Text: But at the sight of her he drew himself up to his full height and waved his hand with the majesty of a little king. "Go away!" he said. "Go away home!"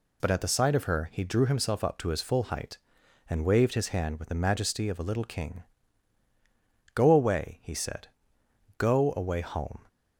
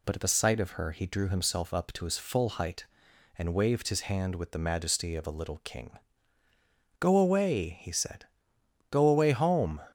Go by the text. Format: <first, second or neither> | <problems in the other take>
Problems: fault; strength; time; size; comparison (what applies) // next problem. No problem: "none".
neither | none